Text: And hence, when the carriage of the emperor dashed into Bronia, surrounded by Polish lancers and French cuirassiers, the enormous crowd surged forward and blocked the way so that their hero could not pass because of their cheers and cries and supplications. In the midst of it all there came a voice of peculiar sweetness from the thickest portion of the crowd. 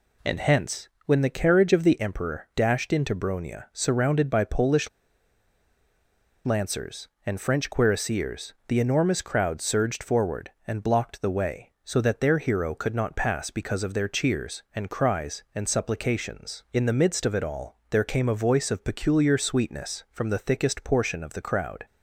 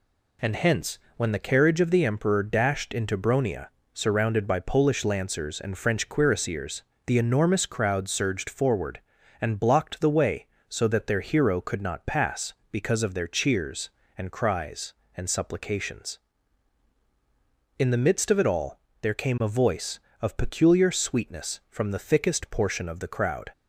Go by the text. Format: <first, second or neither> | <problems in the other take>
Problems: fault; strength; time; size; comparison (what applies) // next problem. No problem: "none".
second | pauses between "Polish" and "lancers"; strong; at 4.8 s; 1.5 s long // pauses between "all" and "there"; slight; at 17.7 s; 0.16 s long; slight in the second